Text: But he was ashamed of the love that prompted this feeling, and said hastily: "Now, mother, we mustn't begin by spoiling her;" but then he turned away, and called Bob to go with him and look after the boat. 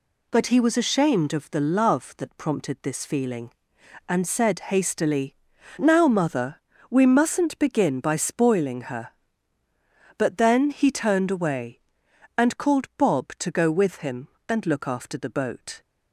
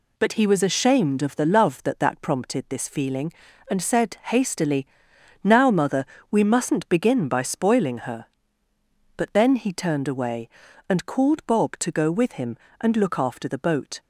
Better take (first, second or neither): first